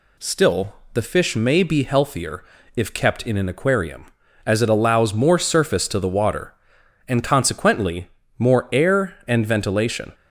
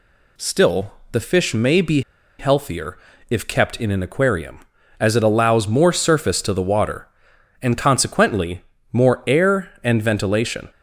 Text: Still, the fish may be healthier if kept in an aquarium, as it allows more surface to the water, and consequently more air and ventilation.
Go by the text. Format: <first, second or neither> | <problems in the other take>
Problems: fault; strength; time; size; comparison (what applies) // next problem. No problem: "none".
first | pauses between "be" and "healthier"; at 2.0 s; 0.38 s long // pauses between "healthier" and "if"; slight; at 2.9 s; 0.32 s long; slight in the first // pauses between "consequently" and "more"; slight; at 8.6 s; 0.30 s long; slight in the first